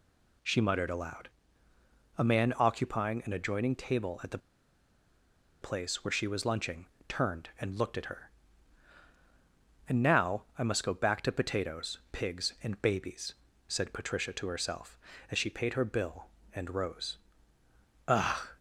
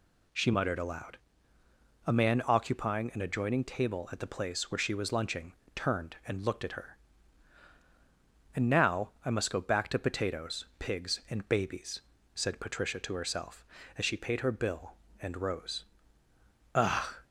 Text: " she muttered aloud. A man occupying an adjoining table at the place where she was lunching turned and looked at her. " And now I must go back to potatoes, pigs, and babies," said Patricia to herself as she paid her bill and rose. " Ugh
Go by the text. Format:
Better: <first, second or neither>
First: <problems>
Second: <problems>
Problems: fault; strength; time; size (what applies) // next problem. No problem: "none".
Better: second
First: pauses between "the" and "place"; at 4.3 s; 1.2 s long // pauses between "lunching" and "turned"; slight; at 6.8 s; 0.20 s long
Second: pauses between "lunching" and "turned"; slight; at 5.5 s; 0.20 s long